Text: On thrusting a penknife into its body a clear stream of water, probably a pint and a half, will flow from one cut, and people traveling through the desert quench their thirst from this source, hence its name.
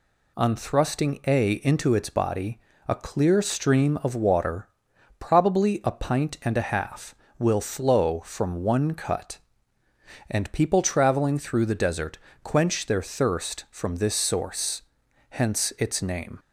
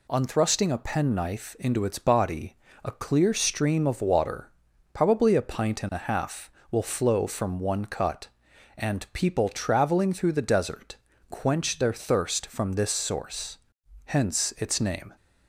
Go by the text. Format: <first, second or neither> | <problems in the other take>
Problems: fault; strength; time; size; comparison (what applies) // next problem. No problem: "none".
second | skips "penknife"; at 1.5 s // pauses between "body" and "a"; slight; at 2.5 s; 0.28 s long; slight in the second // pauses between "desert" and "quench"; slight; at 12.1 s; 0.24 s long; slight in the second